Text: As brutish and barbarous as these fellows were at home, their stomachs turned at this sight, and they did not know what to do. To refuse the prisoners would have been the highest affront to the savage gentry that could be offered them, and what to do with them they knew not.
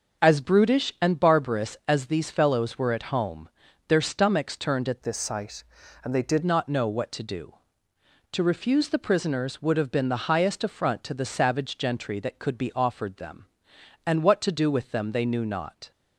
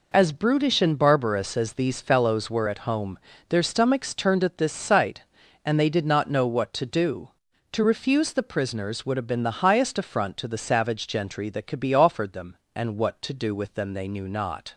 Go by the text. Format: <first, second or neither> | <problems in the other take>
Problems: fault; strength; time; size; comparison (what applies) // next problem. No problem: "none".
second | starts louder than the rest; until 1.2 s; 6.5 dB // changes voice from "this" to "did"; from 5.0 to 6.4 s; 1.4 s long